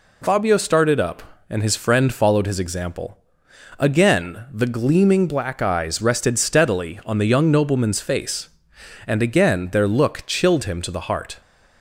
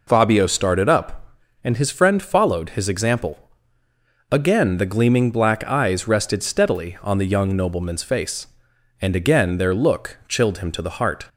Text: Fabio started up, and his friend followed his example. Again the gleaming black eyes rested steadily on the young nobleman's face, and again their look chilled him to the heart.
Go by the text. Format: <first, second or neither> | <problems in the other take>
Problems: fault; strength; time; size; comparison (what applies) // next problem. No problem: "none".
neither | none